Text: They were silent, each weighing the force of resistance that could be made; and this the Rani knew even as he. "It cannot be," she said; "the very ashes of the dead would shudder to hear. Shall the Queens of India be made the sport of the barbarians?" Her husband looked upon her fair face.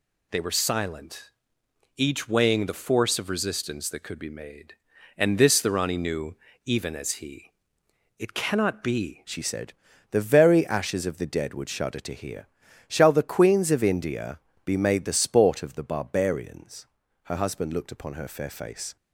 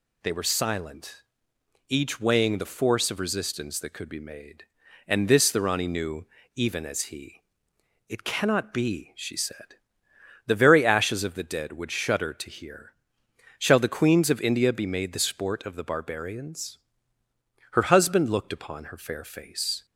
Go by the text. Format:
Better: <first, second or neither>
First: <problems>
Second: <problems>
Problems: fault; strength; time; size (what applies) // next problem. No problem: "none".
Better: second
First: pauses between "knew" and "even"; slight; at 6.3 s; 0.30 s long // changes voice at "she"; from 9.2 s on; 9.7 s long // pauses between "India" and "be"; slight; at 14.3 s; 0.26 s long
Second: pauses between "knew" and "even"; slight; at 6.2 s; 0.30 s long